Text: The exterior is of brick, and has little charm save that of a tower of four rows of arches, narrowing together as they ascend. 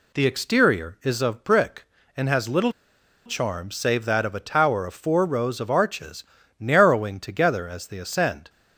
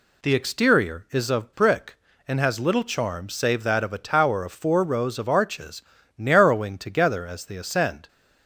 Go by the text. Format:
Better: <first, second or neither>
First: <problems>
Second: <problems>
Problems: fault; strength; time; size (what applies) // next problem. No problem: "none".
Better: second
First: pauses between "little" and "charm"; noticeable; at 2.7 s; 0.53 s long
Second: none